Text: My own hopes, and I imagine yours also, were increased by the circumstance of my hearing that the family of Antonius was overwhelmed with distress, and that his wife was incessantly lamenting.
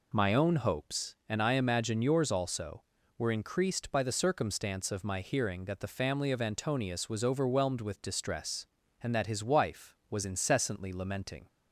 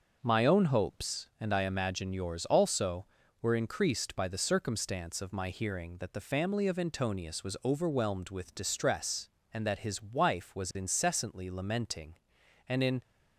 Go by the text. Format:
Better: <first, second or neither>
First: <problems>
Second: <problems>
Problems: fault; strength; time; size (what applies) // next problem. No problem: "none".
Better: first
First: none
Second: starts louder than the rest; until 1.2 s; 6 dB // goes on to say "And in"; slight; from 12.6 s on; 0.34 s long